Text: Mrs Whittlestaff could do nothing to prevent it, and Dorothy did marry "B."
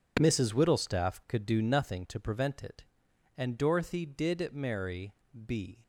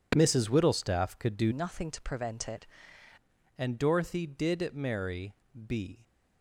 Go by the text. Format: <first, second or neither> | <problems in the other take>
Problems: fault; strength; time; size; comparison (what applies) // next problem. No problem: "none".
first | changes voice from "nothing" to "it"; from 1.5 to 2.6 s; 1.1 s long // pauses between "marry" and "B"; slight; at 5.3 s; 0.32 s long; slight in the first